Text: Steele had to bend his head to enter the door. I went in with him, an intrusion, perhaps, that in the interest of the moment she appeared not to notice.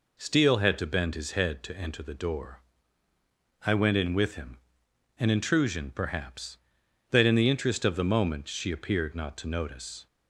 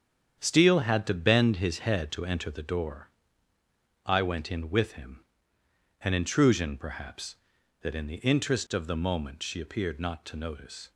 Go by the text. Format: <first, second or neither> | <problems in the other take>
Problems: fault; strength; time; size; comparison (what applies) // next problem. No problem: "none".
first | gets quieter; strong; throughout; 8.5 dB